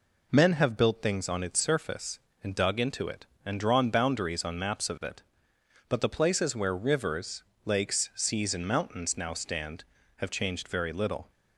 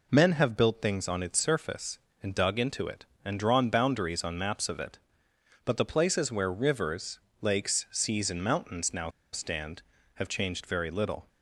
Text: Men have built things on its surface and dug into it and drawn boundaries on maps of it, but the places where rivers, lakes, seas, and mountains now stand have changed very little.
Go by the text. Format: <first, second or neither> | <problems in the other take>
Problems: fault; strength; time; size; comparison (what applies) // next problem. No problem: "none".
first | pauses between "now" and "stand"; slight; at 9.0 s; 0.24 s long